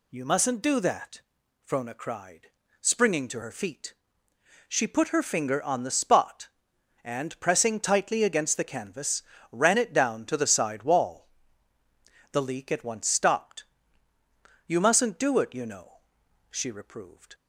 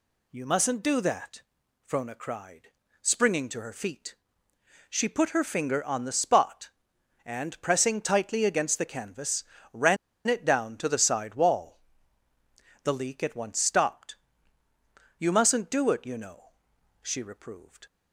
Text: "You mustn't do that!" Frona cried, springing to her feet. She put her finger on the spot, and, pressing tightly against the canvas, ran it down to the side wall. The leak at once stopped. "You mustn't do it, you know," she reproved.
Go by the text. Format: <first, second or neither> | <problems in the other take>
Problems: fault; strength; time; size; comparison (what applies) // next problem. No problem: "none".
first | pauses between "ran" and "it"; slight; at 9.9 s; 0.31 s long